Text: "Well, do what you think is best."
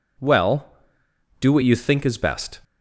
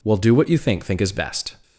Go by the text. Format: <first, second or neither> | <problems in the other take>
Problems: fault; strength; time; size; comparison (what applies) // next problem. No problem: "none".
first | says "think" twice; at 0.8 s